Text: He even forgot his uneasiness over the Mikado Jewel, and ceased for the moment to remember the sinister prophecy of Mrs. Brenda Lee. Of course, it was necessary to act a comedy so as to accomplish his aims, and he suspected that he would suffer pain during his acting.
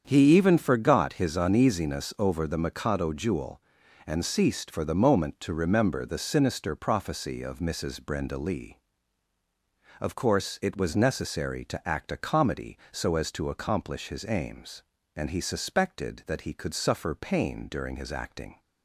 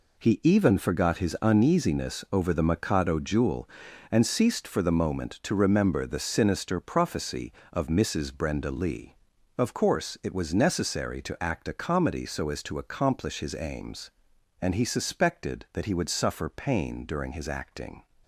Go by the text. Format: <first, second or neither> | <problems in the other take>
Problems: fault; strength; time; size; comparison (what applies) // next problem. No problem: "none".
second | starts louder than the rest; strong; until 1.0 s; 7.5 dB // says "could" for "would"; at 16.5 s